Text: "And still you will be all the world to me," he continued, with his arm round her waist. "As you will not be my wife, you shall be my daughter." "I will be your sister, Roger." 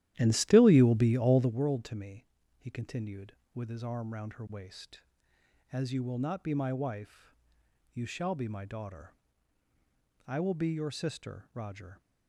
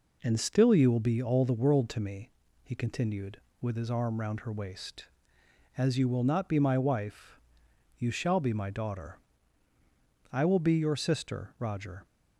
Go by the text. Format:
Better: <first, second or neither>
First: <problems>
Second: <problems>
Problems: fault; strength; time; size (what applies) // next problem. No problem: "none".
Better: second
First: starts louder than the rest; strong; until 1.6 s; 12.5 dB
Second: none